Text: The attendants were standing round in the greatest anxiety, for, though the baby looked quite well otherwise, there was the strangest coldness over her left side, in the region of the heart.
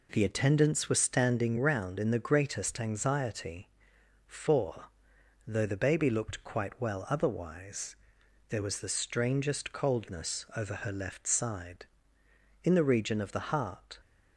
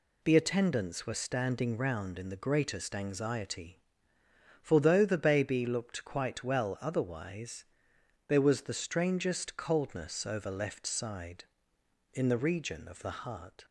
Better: first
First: none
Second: skips "her"; at 10.5 s

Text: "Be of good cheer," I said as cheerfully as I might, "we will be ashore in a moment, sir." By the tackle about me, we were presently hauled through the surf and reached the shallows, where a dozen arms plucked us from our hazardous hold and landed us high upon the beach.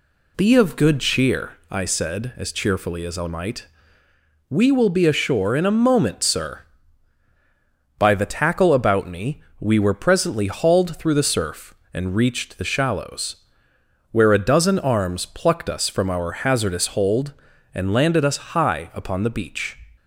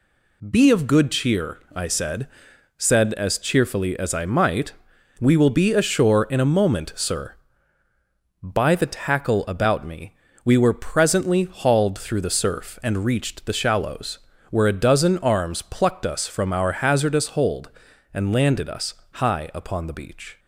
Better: first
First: none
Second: says "said" twice; at 2.7 s // pauses between "us" and "high"; slight; at 18.9 s; 0.16 s long

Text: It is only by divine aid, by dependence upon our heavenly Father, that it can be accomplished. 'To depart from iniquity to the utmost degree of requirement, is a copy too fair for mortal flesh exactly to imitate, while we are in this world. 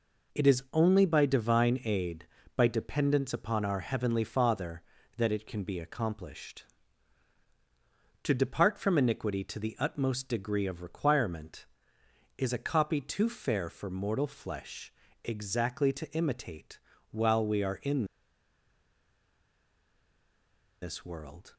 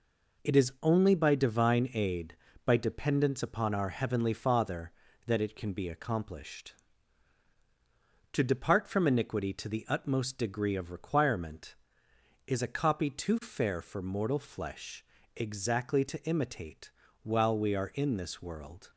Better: second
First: pauses between "flesh" and "exactly"; slight; at 14.9 s; 0.32 s long // pauses between "in" and "this"; strong; at 18.0 s; 2.7 s long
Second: pauses between "flesh" and "exactly"; slight; at 15.0 s; 0.32 s long

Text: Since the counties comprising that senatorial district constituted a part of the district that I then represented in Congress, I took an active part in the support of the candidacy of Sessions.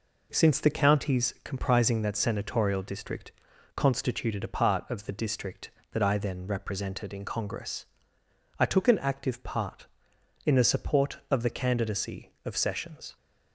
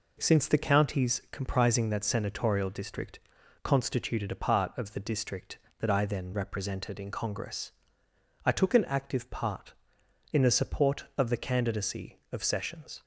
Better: neither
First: pauses between "district" and "constituted"; at 3.3 s; 0.42 s long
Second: pauses between "district" and "constituted"; at 3.2 s; 0.42 s long

